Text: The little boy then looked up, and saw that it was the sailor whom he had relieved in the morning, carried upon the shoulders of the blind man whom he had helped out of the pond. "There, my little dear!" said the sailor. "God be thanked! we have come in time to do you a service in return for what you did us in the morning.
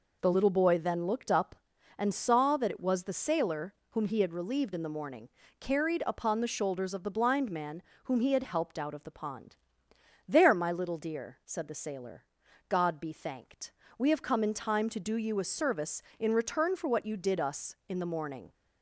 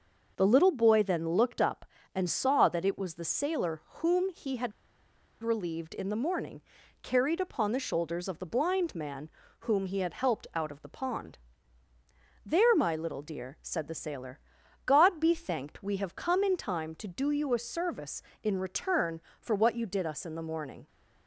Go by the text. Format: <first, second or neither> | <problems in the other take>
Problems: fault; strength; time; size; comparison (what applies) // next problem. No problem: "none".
first | pauses between "sailor" and "whom"; slight; at 3.8 s; 0.18 s long; slight in the first // pauses between "had" and "relieved"; noticeable; at 4.7 s; 0.70 s long // pauses between "man" and "whom"; slight; at 9.3 s; 0.30 s long; slight in the first